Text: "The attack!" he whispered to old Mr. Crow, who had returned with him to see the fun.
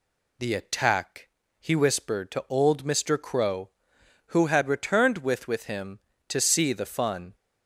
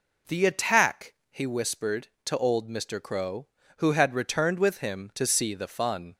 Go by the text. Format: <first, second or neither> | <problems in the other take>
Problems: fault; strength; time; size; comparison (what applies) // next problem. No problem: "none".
second | says "with" twice; at 5.4 s